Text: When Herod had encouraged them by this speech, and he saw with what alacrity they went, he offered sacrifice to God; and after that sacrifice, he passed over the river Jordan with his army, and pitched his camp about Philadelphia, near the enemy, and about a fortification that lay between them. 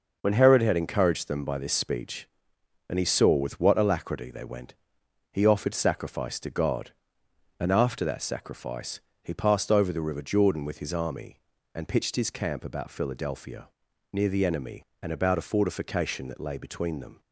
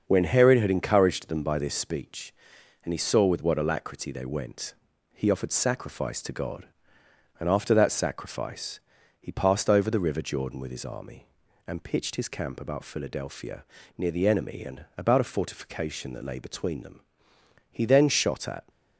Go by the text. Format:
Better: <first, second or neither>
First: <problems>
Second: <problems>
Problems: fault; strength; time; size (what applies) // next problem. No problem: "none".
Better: first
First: none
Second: starts louder than the rest; until 1.0 s; 6.5 dB // goes on to say "He then shot at"; noticeable; from 17.7 s on; 0.90 s long